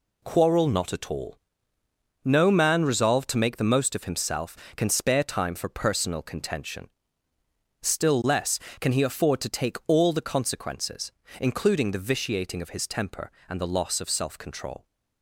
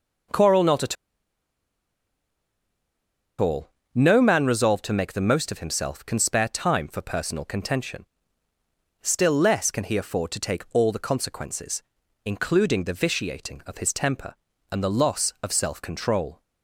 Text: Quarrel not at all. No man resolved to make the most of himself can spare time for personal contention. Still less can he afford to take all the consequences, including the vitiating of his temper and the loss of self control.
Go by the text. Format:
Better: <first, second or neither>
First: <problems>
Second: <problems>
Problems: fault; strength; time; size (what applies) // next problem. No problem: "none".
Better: first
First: none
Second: pauses between "at" and "all"; strong; at 0.9 s; 2.4 s long